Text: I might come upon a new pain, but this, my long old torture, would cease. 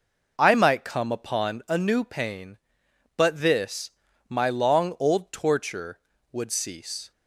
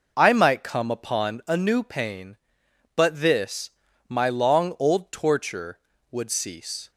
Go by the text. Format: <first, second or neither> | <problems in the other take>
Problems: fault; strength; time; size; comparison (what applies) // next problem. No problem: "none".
neither | none